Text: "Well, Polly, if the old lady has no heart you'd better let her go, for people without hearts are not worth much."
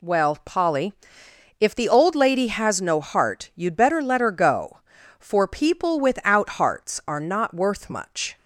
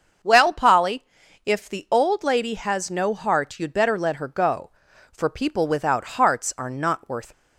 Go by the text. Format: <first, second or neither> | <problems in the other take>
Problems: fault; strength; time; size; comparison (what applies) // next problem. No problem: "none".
first | starts louder than the rest; until 1.6 s; 6.5 dB // stops before "much"; at 7.3 s